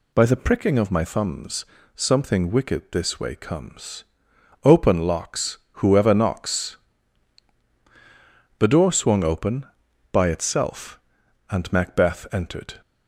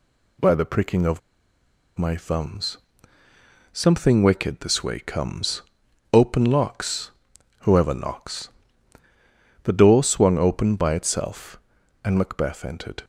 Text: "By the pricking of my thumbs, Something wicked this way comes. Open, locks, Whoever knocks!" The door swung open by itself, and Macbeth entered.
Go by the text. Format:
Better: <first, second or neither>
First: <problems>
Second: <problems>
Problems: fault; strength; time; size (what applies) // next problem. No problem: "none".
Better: first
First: none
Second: pauses between "of" and "my"; noticeable; at 1.1 s; 0.78 s long